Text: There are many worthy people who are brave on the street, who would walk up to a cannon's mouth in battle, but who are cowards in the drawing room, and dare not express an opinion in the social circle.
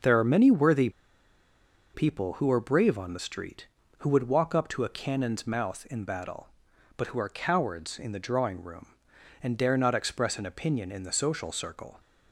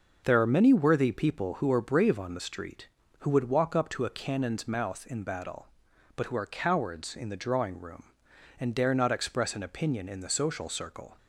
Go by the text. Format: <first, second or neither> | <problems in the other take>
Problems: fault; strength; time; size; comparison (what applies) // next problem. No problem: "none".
second | starts louder than the rest; until 2.0 s; 6 dB // pauses between "worthy" and "people"; at 0.8 s; 1.0 s long